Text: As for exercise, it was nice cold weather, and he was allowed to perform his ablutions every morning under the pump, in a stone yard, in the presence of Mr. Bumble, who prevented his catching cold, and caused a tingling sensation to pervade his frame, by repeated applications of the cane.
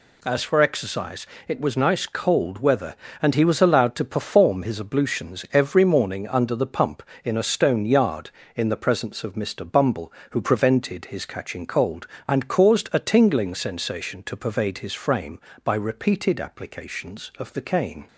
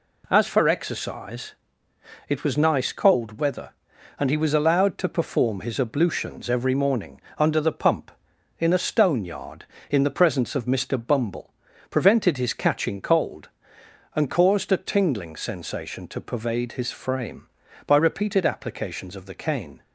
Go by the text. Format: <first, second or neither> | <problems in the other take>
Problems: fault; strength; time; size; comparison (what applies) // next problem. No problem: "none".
first | pauses between "morning" and "under"; slight; at 7.2 s; 0.16 s long // skips "who"; at 11.7 s